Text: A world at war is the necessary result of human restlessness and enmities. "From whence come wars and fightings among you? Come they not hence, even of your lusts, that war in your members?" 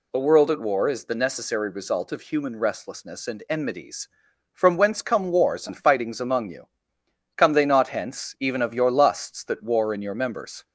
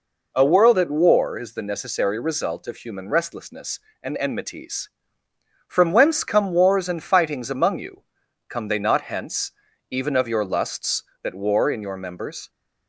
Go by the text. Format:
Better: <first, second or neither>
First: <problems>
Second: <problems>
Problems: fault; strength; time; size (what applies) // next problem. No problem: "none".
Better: neither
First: none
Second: none